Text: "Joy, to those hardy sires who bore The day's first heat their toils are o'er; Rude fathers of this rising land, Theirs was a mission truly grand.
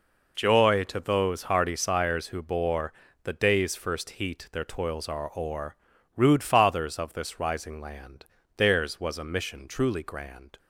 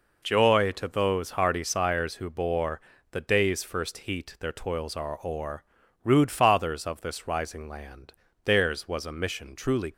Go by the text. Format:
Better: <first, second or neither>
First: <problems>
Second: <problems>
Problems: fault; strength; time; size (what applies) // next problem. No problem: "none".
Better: first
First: pauses between "bore" and "The"; slight; at 2.9 s; 0.32 s long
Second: pauses between "bore" and "The"; slight; at 2.7 s; 0.32 s long // stops before "grand"; at 9.9 s